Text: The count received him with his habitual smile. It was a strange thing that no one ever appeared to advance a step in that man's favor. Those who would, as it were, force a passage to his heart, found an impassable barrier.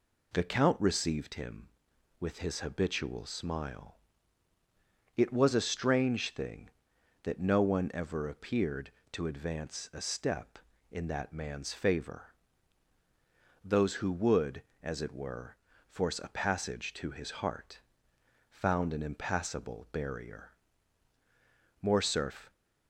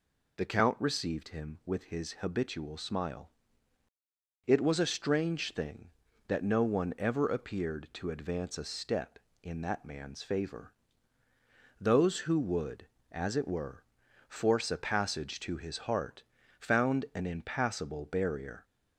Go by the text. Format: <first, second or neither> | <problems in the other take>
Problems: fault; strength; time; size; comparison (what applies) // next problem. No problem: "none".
second | goes on to say "Morcerf"; noticeable; from 21.8 s on; 0.70 s long